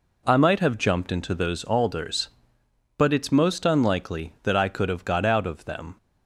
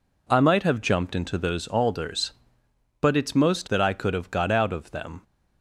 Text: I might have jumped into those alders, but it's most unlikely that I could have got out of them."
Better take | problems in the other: first | skips "unlikely"; at 3.6 s

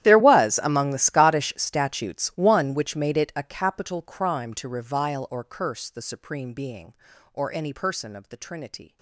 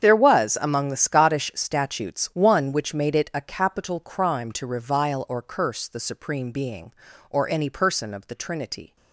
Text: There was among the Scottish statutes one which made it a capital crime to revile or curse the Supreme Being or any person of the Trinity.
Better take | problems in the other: second | gets quieter; strong; throughout; 22.5 dB // starts louder than the rest; strong; until 1.0 s; 12 dB; strong in the second

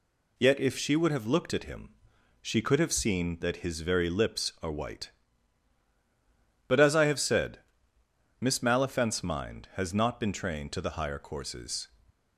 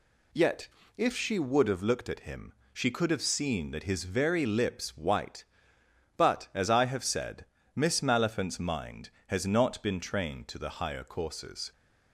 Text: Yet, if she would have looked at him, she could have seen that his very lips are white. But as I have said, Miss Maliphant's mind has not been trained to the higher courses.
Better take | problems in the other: first | skips "are"; at 4.9 s

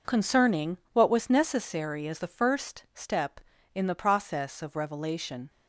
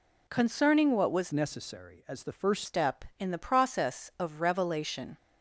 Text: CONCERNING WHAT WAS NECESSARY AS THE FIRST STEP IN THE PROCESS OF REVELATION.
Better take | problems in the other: first | changes voice from "NECESSARY" to "FIRST"; from 1.3 to 2.6 s; 1.3 s long

